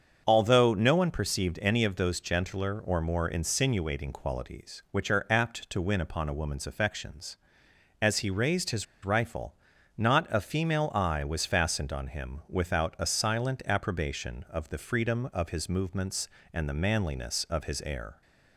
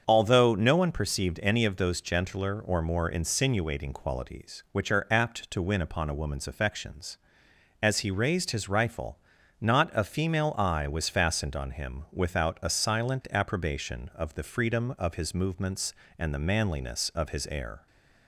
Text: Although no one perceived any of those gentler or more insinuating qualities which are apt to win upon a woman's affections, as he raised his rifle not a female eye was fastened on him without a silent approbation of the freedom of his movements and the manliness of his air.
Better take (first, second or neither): second